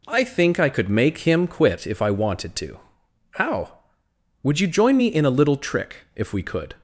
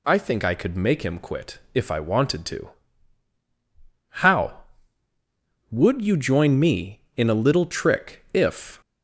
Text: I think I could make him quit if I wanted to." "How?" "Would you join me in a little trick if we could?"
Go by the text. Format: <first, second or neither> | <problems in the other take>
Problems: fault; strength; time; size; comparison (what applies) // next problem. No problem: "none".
first | pauses between "quit" and "if"; slight; at 1.5 s; 0.16 s long // stops before "we could"; at 8.8 s